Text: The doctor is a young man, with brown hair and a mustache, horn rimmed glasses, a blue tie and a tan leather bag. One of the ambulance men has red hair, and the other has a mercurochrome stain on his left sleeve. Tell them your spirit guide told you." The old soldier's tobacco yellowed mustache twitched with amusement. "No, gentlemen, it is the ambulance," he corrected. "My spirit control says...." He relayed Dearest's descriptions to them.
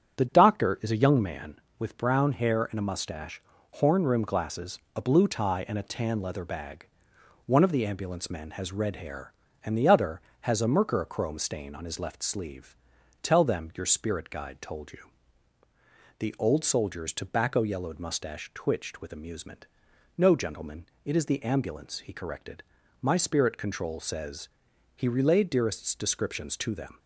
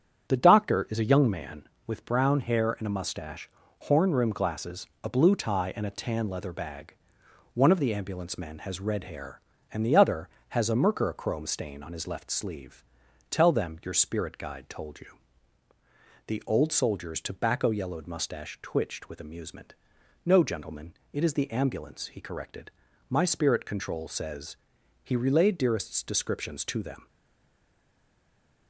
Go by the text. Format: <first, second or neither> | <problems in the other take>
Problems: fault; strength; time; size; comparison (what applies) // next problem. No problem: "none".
first | starts louder than the rest; strong; until 1.3 s; 8.5 dB; strong in the first // stays silent after the last word; noticeable; from 27.0 s on; 1.6 s long